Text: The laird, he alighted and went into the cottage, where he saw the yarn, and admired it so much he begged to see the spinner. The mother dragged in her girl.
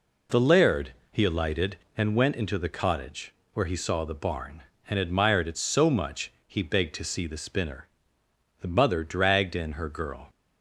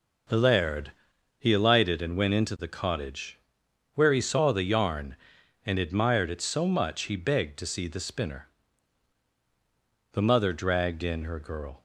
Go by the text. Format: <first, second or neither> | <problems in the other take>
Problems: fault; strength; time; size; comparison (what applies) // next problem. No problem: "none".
second | says "barn" for "yarn"; at 4.1 s